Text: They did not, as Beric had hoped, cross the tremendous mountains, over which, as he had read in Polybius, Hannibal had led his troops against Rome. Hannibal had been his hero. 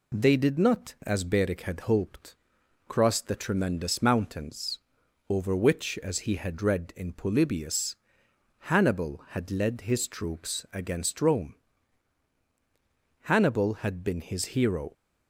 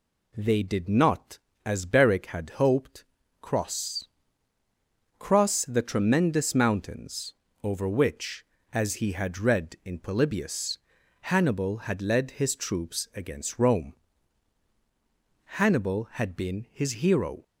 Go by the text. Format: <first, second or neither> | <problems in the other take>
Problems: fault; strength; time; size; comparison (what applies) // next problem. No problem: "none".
first | says "cross" twice; at 5.1 s